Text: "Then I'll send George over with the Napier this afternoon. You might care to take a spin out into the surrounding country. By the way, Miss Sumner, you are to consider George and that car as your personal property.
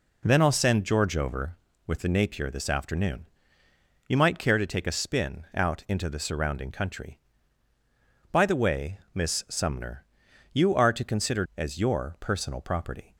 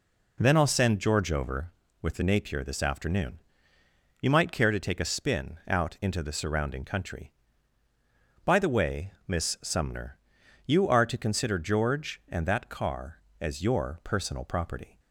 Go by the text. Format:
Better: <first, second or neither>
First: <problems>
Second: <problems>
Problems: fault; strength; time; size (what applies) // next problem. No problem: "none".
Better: second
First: skips "George and that car"; at 11.5 s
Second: none